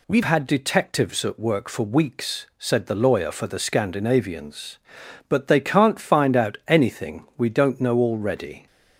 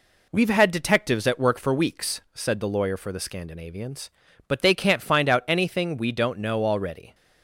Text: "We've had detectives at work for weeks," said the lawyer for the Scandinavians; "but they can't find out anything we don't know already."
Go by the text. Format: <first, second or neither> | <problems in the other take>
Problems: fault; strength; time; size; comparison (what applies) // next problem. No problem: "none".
second | changes voice at "had"; from 0.2 s on; 8.4 s long